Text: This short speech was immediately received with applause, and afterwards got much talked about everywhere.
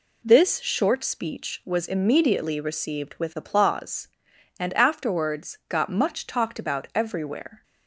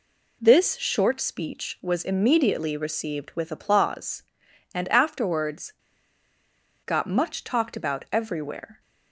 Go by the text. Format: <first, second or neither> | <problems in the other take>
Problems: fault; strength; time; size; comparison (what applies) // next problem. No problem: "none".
first | pauses between "afterwards" and "got"; at 5.7 s; 1.1 s long